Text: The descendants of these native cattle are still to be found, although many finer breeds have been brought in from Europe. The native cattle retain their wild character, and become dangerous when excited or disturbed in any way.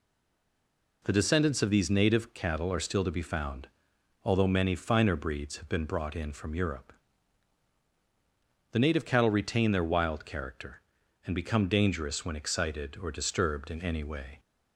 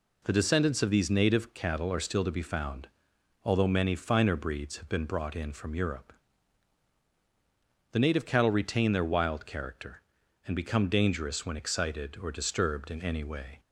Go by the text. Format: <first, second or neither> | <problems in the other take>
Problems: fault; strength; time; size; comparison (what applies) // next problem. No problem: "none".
second | stays silent before the first word; until 1.0 s; 1.0 s long